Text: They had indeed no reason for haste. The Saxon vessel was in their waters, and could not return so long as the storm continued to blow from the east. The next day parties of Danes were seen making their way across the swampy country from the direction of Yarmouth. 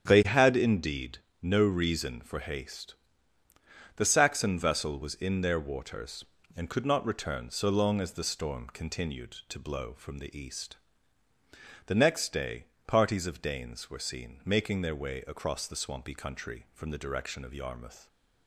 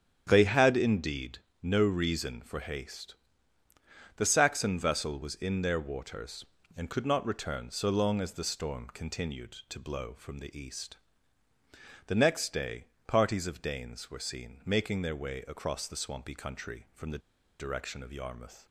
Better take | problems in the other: first | starts louder than the rest; strong; until 1.2 s; 9 dB; strong in the first // pauses between "indeed" and "no"; slight; at 1.3 s; 0.24 s long; slight in the first // pauses between "day" and "parties"; slight; at 12.8 s; 0.22 s long; slight in the first // pauses between "the" and "direction"; at 17.2 s; 0.40 s long

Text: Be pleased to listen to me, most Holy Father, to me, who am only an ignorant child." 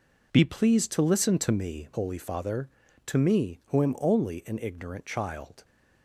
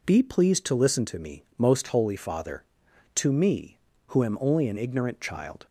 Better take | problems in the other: second | skips "most"; at 1.9 s

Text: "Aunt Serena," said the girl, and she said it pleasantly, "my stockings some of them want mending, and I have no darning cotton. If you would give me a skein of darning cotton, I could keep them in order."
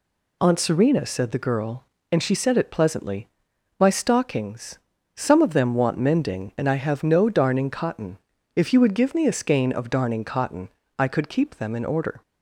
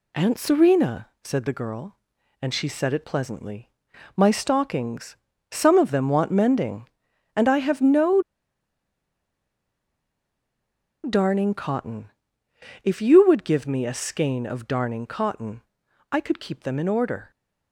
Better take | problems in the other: first | pauses between "stockings" and "some"; slight; at 5.1 s; 0.36 s long; slight in the first // pauses between "no" and "darning"; strong; at 8.2 s; 2.8 s long

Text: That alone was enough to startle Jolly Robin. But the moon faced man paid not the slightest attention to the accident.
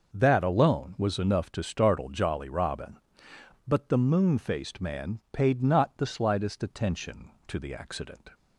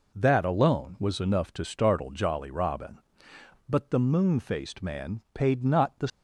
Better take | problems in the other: first | stops before "slightest attention to the accident"; at 6.0 s

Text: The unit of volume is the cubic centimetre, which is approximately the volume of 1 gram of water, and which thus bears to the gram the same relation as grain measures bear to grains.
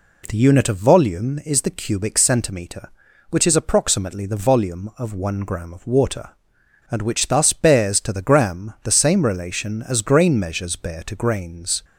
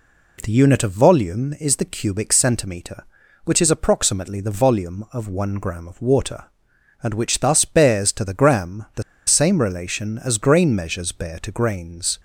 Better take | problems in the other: first | pauses between "the" and "same"; slight; at 9.0 s; 0.24 s long

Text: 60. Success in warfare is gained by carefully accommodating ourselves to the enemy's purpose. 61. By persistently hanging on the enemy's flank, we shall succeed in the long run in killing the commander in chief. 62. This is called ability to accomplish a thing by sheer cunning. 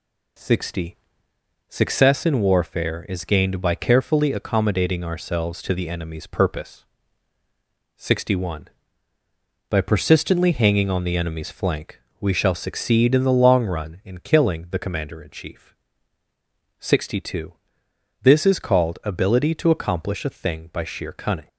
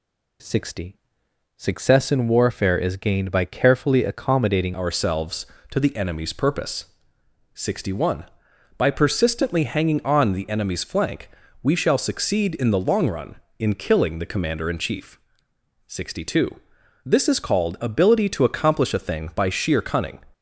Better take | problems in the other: first | changes voice at "ourselves"; from 4.7 s on; 15.5 s long

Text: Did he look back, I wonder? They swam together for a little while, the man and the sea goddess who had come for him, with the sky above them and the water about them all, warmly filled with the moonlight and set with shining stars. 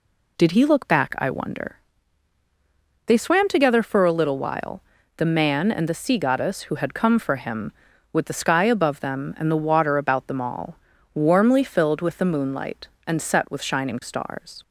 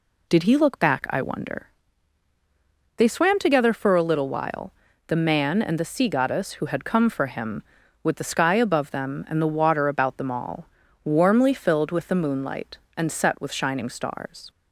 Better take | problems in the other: neither | none

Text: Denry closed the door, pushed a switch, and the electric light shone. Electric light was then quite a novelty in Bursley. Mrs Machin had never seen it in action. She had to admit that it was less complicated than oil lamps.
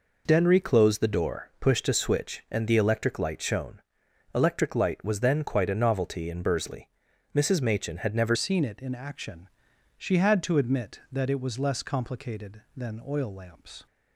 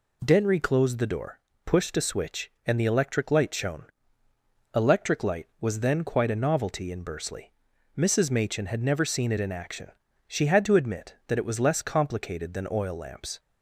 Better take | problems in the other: second | changes voice at "seen"; from 8.3 s on; 5.5 s long

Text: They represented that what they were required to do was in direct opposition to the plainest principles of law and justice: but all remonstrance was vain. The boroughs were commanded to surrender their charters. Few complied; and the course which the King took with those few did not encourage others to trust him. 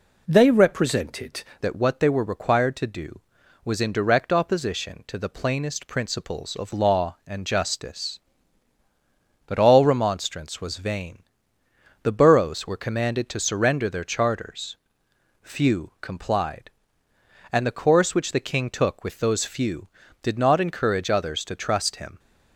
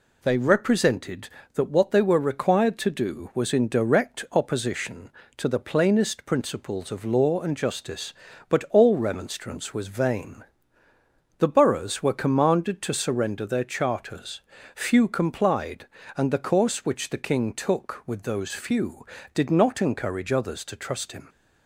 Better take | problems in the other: second | changes voice at "that"; from 1.6 s on; 20.5 s long

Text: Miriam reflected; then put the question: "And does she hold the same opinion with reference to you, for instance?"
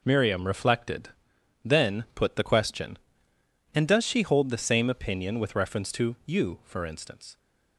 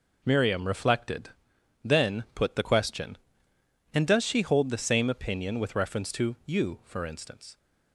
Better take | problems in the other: neither | none

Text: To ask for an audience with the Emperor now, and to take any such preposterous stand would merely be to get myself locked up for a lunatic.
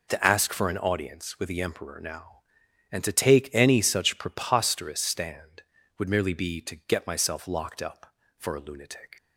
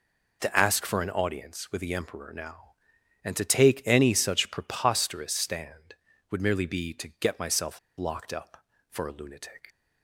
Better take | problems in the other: first | pauses between "myself" and "locked"; slight; at 7.7 s; 0.18 s long

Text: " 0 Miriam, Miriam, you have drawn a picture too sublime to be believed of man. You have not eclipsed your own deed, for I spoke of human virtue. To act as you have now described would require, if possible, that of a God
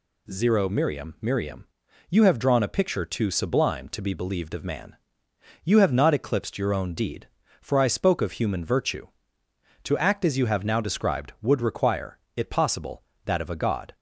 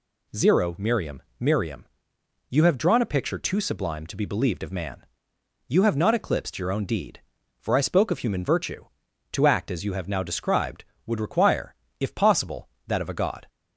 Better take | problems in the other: second | says "it" for "if"; at 12.3 s

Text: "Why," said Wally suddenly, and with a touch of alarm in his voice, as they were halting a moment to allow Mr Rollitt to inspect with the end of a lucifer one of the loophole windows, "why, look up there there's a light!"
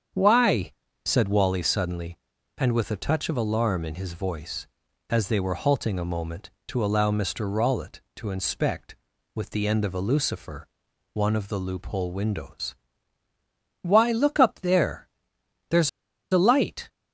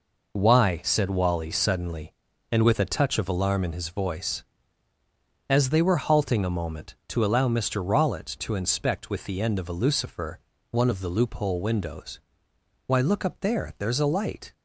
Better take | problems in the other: second | starts louder than the rest; strong; until 1.4 s; 7.5 dB // pauses between "lucifer" and "one"; noticeable; at 10.6 s; 0.46 s long; slight in the second // pauses between "there" and "there's"; noticeable; at 15.0 s; 0.62 s long // pauses between "there's" and "a"; at 15.8 s; 0.42 s long

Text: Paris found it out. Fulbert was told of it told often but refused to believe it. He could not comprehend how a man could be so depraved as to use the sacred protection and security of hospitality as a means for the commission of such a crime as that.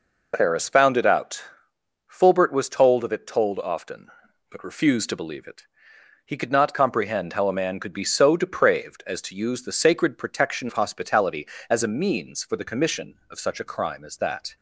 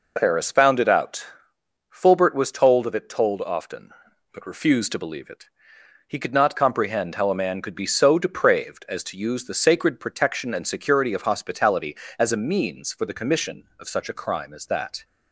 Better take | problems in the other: second | skips "and security"; at 10.6 s

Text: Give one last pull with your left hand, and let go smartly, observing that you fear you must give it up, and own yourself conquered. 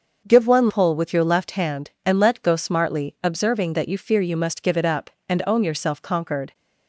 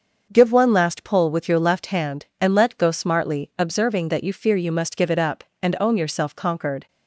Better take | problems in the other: second | starts louder than the rest; until 1.3 s; 6.5 dB; also in the second // skips "last"; at 0.6 s

